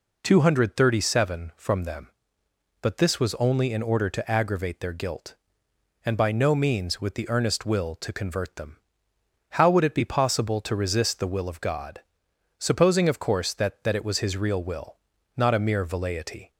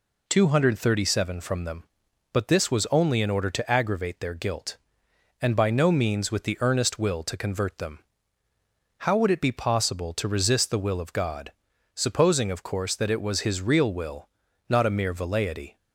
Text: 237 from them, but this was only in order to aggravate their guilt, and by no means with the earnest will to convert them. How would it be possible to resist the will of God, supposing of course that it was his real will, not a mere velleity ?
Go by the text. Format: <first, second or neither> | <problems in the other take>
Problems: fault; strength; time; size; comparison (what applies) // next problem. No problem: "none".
second | says "that" twice; at 13.8 s